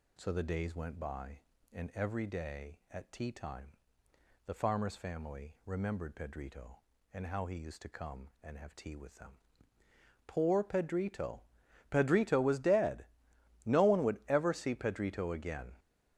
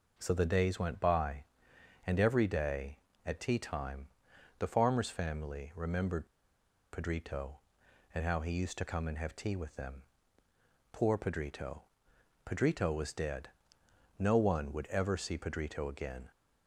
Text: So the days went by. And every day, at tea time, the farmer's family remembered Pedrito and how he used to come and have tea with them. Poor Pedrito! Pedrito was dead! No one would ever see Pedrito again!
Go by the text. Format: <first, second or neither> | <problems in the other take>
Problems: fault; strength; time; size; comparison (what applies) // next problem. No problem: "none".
first | pauses between "remembered" and "Pedrito"; noticeable; at 6.2 s; 0.66 s long